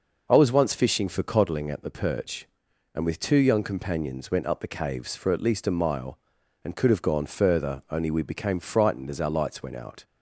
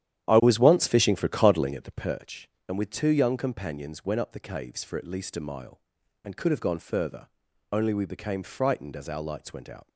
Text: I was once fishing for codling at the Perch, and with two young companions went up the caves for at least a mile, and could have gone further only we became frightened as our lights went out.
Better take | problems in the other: first | starts louder than the rest; strong; until 2.1 s; 10.5 dB // pauses between "further" and "only"; at 7.2 s; 0.40 s long

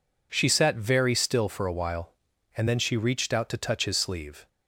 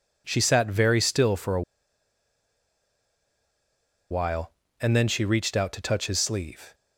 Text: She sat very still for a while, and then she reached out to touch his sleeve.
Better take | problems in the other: first | pauses between "a" and "while"; strong; at 1.6 s; 2.4 s long

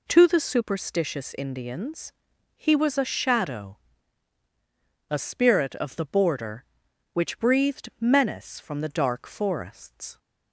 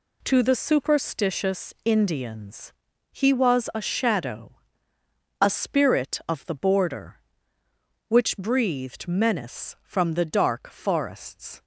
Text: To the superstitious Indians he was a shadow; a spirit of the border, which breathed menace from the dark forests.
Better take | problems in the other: neither | pauses between "Indians" and "he"; the same in both

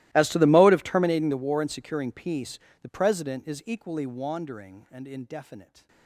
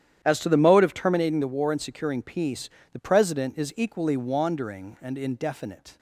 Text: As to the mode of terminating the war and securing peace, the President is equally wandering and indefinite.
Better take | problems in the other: second | gets quieter; strong; throughout; 27 dB // starts louder than the rest; strong; until 1.1 s; 17.5 dB; strong in the second

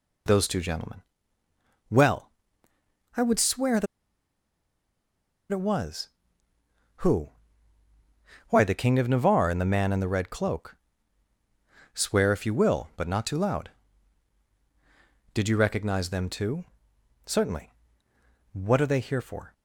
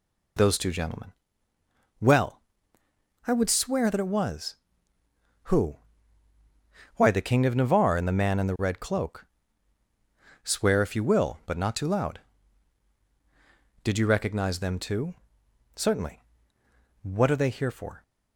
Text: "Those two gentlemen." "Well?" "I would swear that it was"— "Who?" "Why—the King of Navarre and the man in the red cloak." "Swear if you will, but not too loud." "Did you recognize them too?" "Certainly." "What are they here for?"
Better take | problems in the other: second | pauses between "that" and "it"; strong; at 3.8 s; 1.6 s long

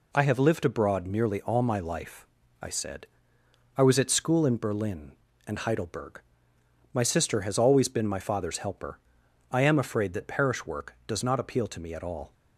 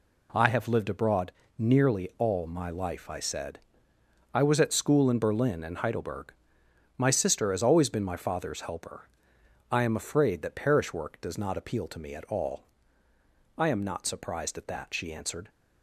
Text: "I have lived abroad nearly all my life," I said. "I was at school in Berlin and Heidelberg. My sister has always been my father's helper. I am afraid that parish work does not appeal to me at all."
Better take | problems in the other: first | pauses between "abroad" and "nearly"; slight; at 1.3 s; 0.26 s long // goes on to say "I am not surprised at that she answered"; strong; from 13.5 s on; 1.9 s long

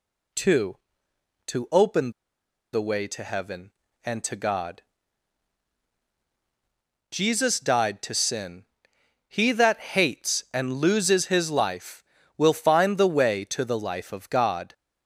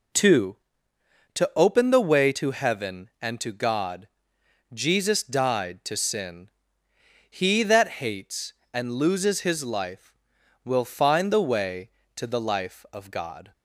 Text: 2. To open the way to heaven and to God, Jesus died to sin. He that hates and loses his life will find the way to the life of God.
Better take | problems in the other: second | pauses between "open" and "the"; noticeable; at 2.1 s; 0.62 s long

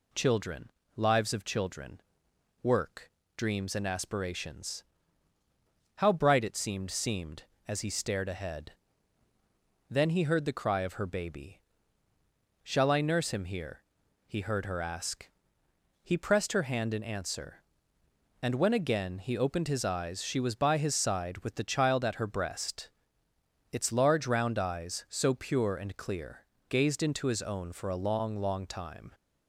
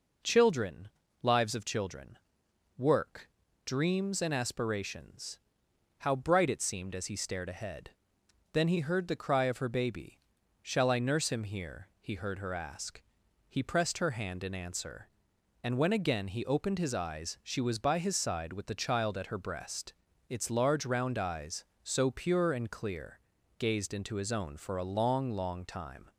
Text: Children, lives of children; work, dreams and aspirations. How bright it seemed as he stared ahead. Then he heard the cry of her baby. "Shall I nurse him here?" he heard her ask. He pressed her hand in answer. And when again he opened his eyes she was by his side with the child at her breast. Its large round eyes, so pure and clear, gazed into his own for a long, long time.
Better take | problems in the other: second | says "seemed" twice; at 6.9 s

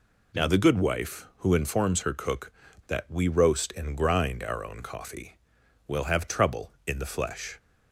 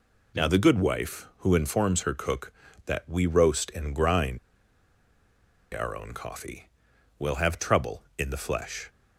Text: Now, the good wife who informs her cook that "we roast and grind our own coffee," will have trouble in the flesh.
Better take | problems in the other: first | pauses between "grind" and "our"; strong; at 4.3 s; 1.3 s long

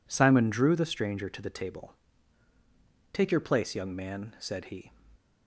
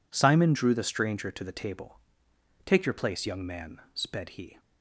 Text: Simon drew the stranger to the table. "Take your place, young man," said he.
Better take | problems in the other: first | says "sped" for "said"; at 3.9 s

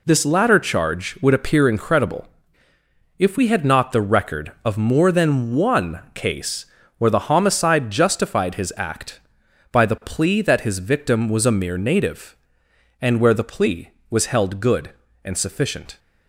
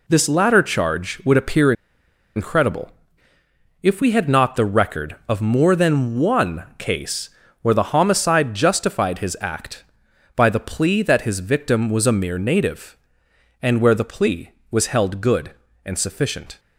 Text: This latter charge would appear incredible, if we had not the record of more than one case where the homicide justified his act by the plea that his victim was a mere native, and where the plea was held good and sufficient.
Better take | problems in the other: first | pauses between "appear" and "incredible"; noticeable; at 1.7 s; 0.63 s long // pauses between "case" and "where"; slight; at 7.2 s; 0.32 s long; slight in the first

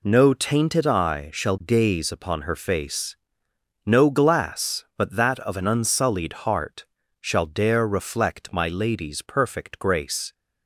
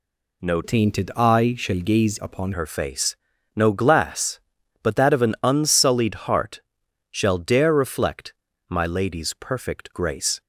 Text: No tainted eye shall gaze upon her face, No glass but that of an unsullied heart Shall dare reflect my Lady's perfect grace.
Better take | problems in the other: first | changes voice from "tainted" to "upon"; from 0.6 to 2.5 s; 1.9 s long // pauses between "heart" and "Shall"; noticeable; at 6.6 s; 0.50 s long; also in the first // pauses between "reflect" and "my"; slight; at 8.3 s; 0.36 s long

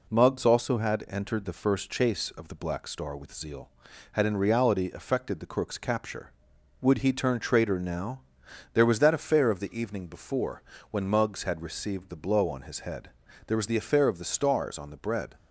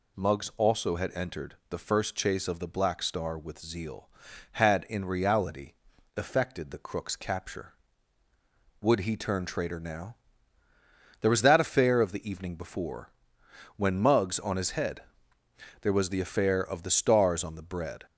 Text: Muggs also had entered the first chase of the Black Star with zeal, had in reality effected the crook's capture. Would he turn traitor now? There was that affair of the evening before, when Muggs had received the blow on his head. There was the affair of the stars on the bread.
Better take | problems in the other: first | pauses between "reality" and "effected"; at 5.7 s; 0.42 s long // skips "had received the blow"; at 14.3 s

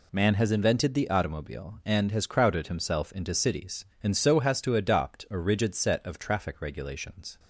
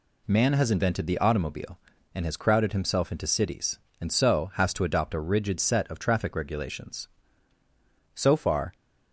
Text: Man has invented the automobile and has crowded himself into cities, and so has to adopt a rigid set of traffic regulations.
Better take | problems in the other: first | goes on to say "So far"; from 8.1 s on; 0.60 s long

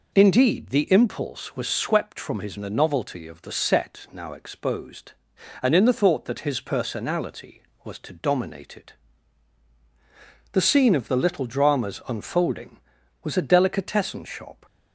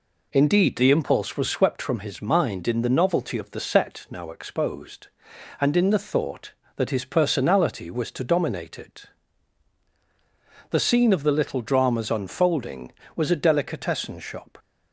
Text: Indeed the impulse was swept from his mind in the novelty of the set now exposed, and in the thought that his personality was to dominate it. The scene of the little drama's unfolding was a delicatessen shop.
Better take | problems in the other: second | skips "mind in"; at 2.5 s

